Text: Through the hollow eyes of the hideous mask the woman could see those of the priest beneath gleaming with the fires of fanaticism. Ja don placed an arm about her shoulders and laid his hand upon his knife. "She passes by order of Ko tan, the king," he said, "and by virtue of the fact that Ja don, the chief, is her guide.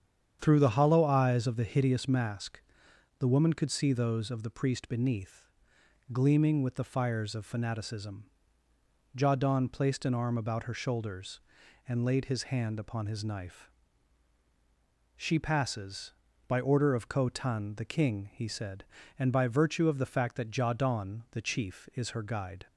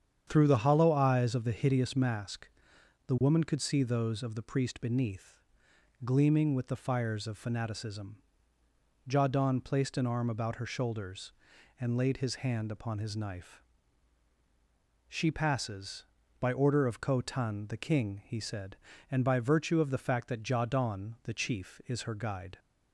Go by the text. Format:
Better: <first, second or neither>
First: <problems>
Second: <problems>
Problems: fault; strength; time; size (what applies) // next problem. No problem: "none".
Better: neither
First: starts louder than the rest; strong; until 1.4 s; 8 dB // pauses between "mask" and "the"; noticeable; at 2.6 s; 0.58 s long // pauses between "beneath" and "gleaming"; noticeable; at 5.4 s; 0.64 s long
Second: starts louder than the rest; strong; until 1.2 s; 8 dB // pauses between "mask" and "the"; noticeable; at 2.4 s; 0.58 s long // pauses between "beneath" and "gleaming"; noticeable; at 5.4 s; 0.64 s long